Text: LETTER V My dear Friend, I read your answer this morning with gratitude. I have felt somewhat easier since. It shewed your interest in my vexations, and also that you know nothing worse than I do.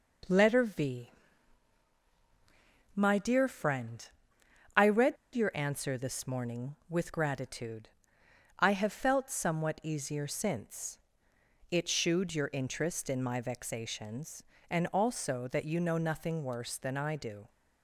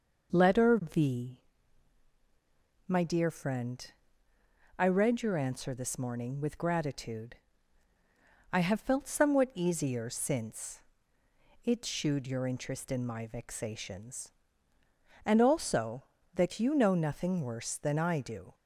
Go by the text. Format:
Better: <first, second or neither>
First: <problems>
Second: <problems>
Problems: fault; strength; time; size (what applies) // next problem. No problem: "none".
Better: second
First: pauses between "V" and "My"; strong; at 1.1 s; 1.8 s long // pauses between "read" and "your"; slight; at 5.1 s; 0.18 s long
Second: pauses between "V" and "My"; strong; at 1.4 s; 1.4 s long